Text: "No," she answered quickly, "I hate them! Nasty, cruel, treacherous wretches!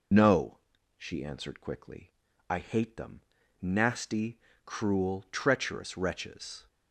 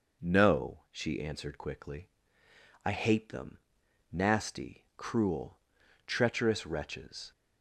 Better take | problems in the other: second | loses the start of "No"; at 0.1 s; 40 ms

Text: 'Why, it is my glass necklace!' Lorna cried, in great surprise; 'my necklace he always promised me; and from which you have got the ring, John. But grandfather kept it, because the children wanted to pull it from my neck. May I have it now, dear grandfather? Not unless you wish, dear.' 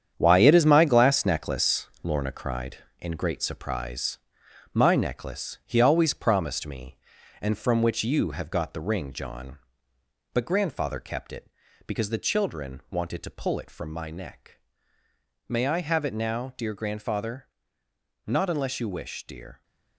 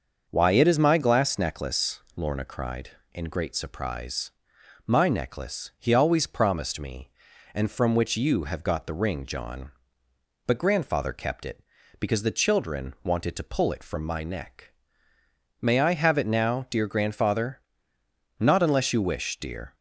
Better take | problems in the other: second | gets quieter; strong; throughout; 9.5 dB // starts louder than the rest; strong; until 1.1 s; 8.5 dB; also in the second

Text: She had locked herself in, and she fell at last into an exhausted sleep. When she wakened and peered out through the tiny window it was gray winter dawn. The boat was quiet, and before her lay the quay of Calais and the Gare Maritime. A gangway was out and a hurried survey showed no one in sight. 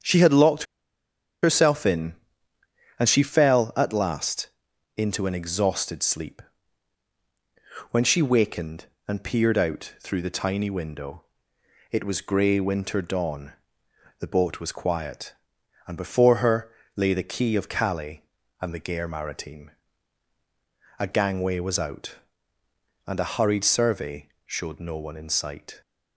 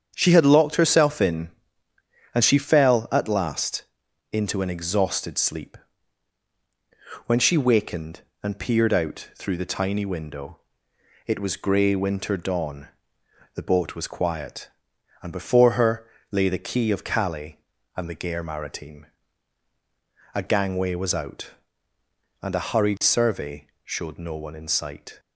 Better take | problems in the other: second | starts louder than the rest; strong; until 1.8 s; 7.5 dB; strong in the second // pauses between "locked" and "herself"; noticeable; at 0.6 s; 0.79 s long // pauses between "last" and "into"; noticeable; at 4.4 s; 0.50 s long; noticeable in the second // pauses between "window" and "it"; noticeable; at 11.2 s; 0.68 s long; noticeable in the second // pauses between "her" and "lay"; slight; at 16.6 s; 0.26 s long; slight in the second // pauses between "survey" and "showed"; slight; at 24.2 s; 0.16 s long; slight in the second

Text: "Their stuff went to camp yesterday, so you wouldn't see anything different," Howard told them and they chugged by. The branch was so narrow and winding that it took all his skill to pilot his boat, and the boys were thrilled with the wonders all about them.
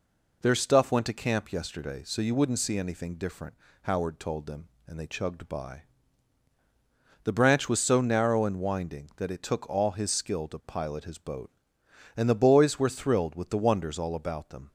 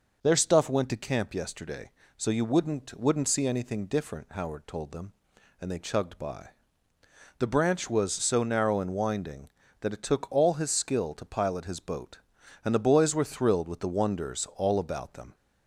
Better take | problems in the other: first | says "wouldn't" twice; at 3.0 s

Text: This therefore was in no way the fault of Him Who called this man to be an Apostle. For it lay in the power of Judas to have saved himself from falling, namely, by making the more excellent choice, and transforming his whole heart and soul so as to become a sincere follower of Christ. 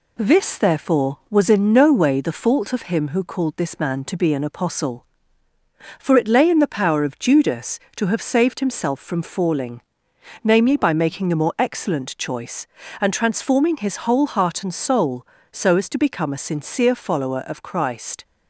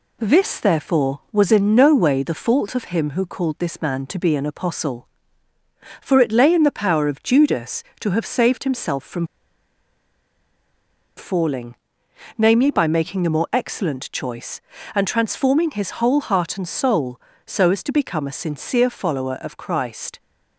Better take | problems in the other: first | pauses between "from" and "falling"; strong; at 9.2 s; 1.9 s long

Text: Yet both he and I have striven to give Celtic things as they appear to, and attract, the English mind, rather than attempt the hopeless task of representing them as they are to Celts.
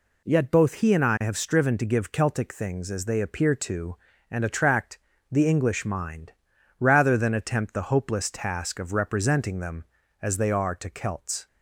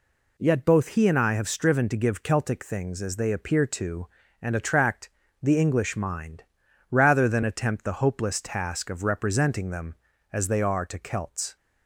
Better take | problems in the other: neither | none

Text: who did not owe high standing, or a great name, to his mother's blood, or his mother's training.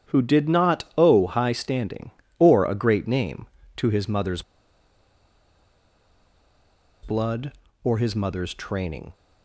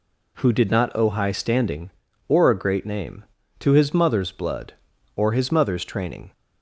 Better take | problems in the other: second | starts louder than the rest; strong; until 1.1 s; 9.5 dB // pauses between "mother's" and "blood"; strong; at 4.4 s; 2.6 s long

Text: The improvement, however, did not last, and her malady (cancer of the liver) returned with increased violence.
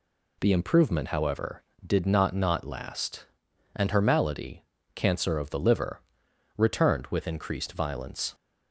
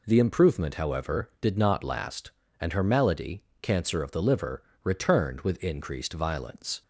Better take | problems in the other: second | says "not" twice; at 2.3 s

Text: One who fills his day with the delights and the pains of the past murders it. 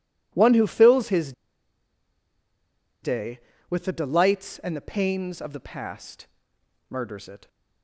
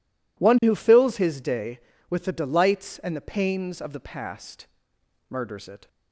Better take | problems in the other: second | pauses between "his" and "day"; strong; at 1.3 s; 1.7 s long // pauses between "past" and "murders"; noticeable; at 6.2 s; 0.64 s long; noticeable in the second

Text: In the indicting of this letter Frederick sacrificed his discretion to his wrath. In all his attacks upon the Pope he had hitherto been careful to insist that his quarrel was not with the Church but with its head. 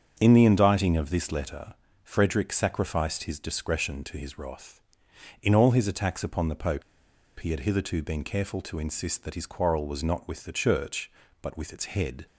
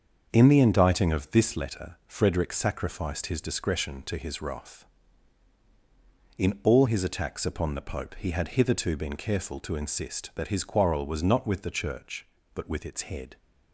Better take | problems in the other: second | starts louder than the rest; strong; until 1.2 s; 7 dB; also in the second // pauses between "letter" and "Frederick"; slight; at 1.7 s; 0.28 s long // pauses between "Pope" and "he"; noticeable; at 6.8 s; 0.56 s long

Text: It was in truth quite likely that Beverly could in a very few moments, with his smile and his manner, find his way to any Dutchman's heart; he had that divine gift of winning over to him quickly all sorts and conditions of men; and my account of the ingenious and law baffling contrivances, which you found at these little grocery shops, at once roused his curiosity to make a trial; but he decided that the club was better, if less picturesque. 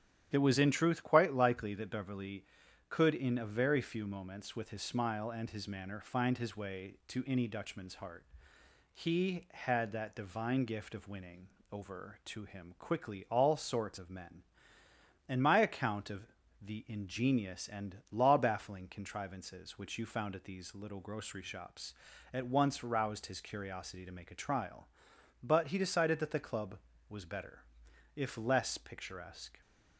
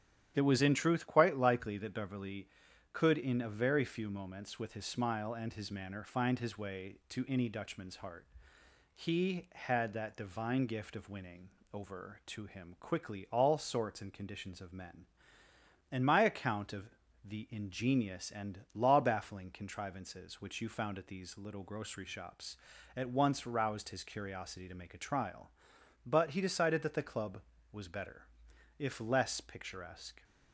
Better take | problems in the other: second | starts louder than the rest; strong; until 1.3 s; 10.5 dB; strong in the second // pauses between "winning" and "over"; slight; at 11.4 s; 0.22 s long; slight in the second // skips "and conditions"; at 13.9 s // pauses between "of" and "the"; slight; at 16.2 s; 0.34 s long; slight in the second

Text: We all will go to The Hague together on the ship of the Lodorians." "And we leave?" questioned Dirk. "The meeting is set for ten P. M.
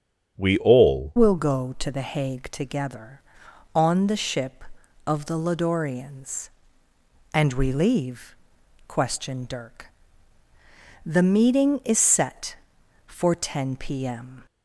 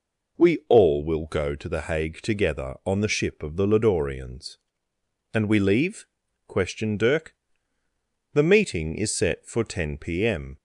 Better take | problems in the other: second | starts louder than the rest; strong; until 1.3 s; 7.5 dB // changes voice at "will"; from 1.1 s on; 13.3 s long

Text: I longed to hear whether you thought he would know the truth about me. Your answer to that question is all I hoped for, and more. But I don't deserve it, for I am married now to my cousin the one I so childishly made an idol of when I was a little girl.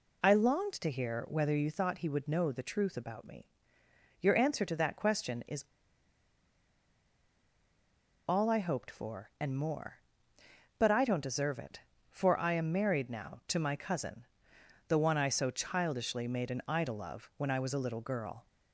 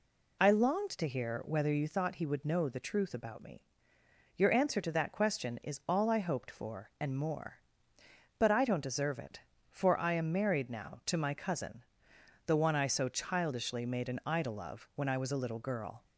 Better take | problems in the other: second | pauses between "is" and "all"; strong; at 5.6 s; 2.6 s long // pauses between "cousin" and "the"; noticeable; at 14.2 s; 0.64 s long; noticeable in the second

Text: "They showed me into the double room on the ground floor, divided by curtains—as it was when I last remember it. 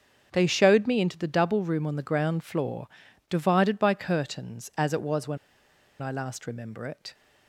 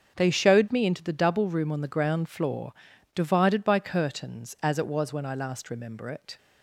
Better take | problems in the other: second | starts louder than the rest; until 1.3 s; 7 dB; also in the second // pauses between "when" and "I"; noticeable; at 5.3 s; 0.63 s long

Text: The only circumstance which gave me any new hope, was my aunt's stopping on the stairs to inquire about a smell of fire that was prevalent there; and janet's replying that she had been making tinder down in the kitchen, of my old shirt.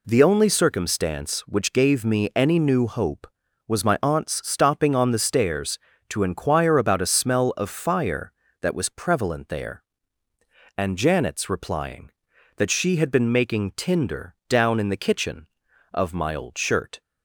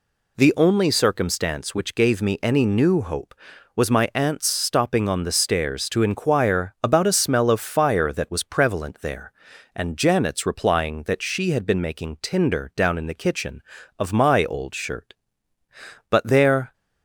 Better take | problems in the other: first | goes on to say "But there"; noticeable; from 16.1 s on; 0.62 s long

